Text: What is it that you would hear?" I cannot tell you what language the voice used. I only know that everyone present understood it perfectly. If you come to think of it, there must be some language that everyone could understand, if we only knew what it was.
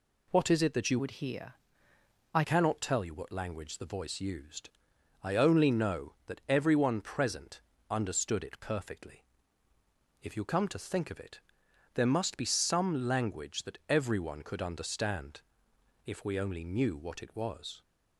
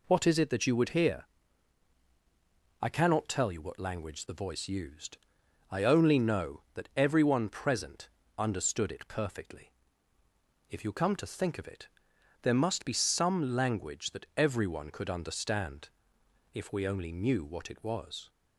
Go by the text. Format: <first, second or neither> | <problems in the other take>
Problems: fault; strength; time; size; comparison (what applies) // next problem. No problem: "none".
second | changes voice from "would" to "I"; from 0.9 to 2.4 s; 1.5 s long // pauses between "present" and "understood"; slight; at 7.6 s; 0.28 s long; slight in the second